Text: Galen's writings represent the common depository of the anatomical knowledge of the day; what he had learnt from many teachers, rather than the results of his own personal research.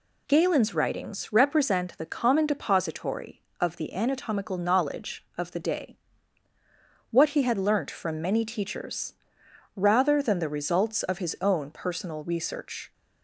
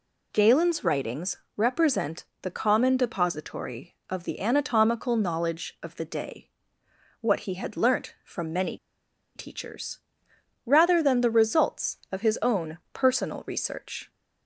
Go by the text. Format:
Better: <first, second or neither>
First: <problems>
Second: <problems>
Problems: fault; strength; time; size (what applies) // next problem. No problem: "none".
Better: first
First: none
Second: pauses between "writings" and "represent"; slight; at 1.3 s; 0.18 s long // pauses between "represent" and "the"; slight; at 2.2 s; 0.20 s long // pauses between "many" and "teachers"; noticeable; at 8.7 s; 0.58 s long // pauses between "own" and "personal"; slight; at 12.7 s; 0.16 s long